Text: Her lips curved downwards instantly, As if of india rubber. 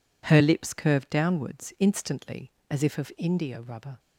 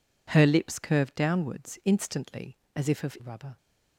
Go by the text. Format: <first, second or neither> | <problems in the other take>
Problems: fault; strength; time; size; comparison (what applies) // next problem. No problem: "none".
first | skips "india"; at 3.1 s